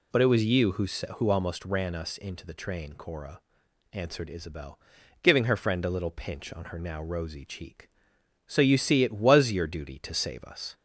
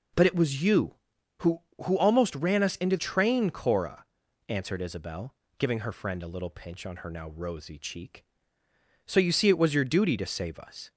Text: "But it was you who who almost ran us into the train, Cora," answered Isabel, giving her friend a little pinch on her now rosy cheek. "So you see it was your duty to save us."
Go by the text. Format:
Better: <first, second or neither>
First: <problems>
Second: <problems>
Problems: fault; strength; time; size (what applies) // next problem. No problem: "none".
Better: first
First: none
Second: skips "the"; at 2.9 s